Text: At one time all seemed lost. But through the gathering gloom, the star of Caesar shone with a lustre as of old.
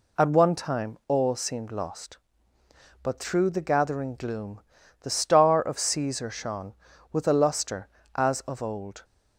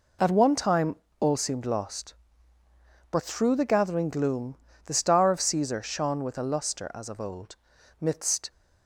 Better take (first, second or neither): first